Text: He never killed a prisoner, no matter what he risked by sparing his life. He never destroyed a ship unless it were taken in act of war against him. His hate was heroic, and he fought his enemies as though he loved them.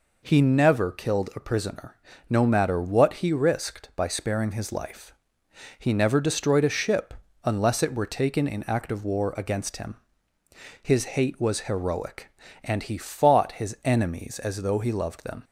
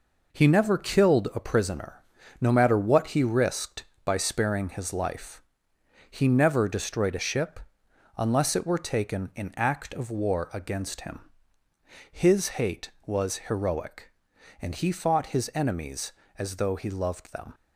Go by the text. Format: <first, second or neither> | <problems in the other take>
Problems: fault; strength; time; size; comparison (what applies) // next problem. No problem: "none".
first | gets quieter; noticeable; throughout; 6 dB // pauses between "ship" and "unless"; noticeable; at 7.6 s; 0.56 s long; slight in the first